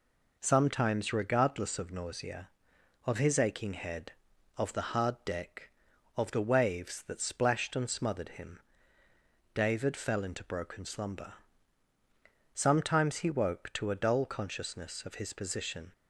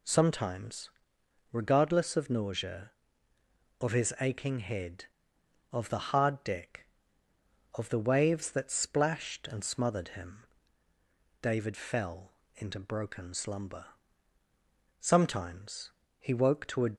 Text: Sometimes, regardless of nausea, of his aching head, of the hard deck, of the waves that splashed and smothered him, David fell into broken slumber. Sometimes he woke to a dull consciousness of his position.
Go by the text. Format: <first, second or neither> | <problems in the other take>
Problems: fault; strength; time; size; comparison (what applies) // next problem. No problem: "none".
first | pauses between "fell" and "into"; slight; at 12.3 s; 0.24 s long // pauses between "Sometimes" and "he"; slight; at 15.9 s; 0.28 s long // stops before "dull consciousness of his position"; at 16.9 s